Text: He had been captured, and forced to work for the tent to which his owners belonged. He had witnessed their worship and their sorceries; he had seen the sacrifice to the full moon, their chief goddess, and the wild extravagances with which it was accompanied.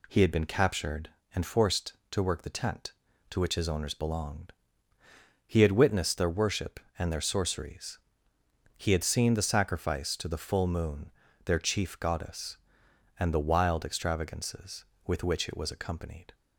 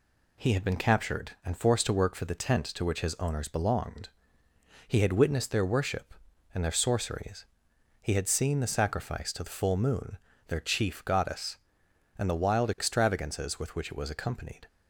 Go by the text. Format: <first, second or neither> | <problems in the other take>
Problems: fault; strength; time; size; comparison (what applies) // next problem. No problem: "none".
second | skips "for"; at 2.4 s